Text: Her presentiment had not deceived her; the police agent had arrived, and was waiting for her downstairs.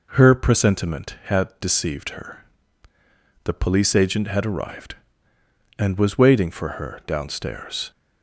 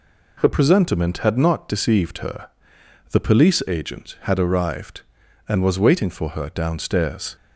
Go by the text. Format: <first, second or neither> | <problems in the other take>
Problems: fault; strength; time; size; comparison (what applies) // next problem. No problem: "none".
second | skips "not"; at 1.5 s